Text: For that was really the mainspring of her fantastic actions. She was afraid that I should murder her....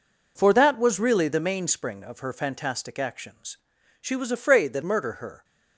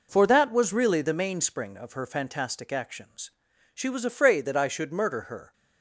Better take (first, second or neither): second